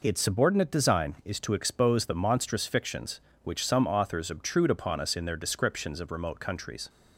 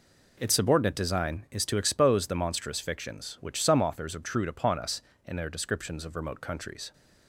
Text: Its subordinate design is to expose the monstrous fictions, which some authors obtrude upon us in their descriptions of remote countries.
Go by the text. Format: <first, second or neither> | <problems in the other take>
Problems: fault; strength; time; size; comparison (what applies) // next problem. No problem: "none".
neither | none